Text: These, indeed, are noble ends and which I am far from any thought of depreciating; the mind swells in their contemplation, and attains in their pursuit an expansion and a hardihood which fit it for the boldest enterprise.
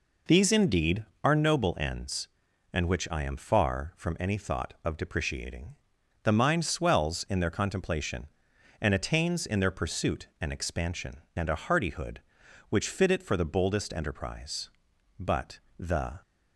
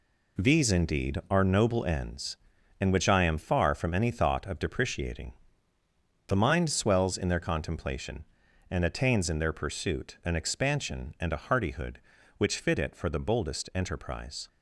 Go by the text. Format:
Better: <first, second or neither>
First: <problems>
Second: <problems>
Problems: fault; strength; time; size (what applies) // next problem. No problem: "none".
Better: second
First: goes on to say "But the"; noticeable; from 15.1 s on; 1.0 s long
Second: none